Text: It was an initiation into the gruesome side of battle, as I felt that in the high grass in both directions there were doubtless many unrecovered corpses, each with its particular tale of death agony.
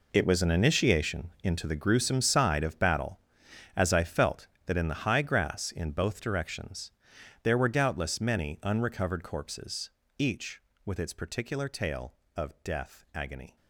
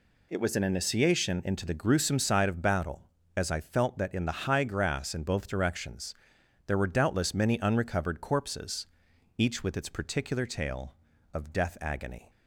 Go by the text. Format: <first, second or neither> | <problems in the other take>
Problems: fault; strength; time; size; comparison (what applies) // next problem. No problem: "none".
second | gets quieter; strong; throughout; 13 dB // pauses between "directions" and "there"; noticeable; at 6.9 s; 0.52 s long; noticeable in the second